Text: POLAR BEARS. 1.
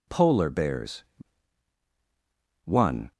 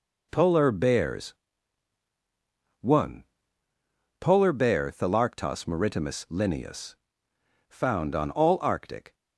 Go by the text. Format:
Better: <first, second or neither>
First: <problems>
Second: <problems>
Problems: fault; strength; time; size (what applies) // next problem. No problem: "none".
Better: first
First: none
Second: goes on to say "POLAR BEAR Thalarctos maritimus Linnaeus Found on all Arctic"; strong; from 4.2 s on; 4.9 s long